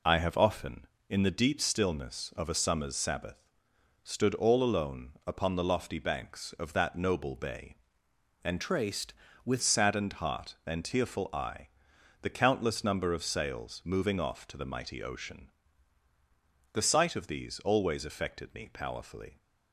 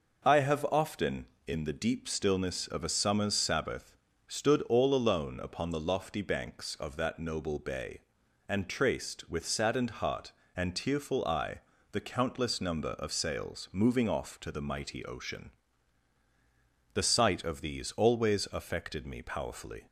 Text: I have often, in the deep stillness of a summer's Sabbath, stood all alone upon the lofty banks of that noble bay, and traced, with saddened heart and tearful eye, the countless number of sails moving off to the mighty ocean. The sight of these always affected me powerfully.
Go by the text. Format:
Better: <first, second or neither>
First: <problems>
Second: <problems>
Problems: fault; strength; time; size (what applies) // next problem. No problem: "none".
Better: second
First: pauses between "alone" and "upon"; slight; at 5.1 s; 0.16 s long // changes voice from "traced" to "with"; from 8.5 to 9.6 s; 1.1 s long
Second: none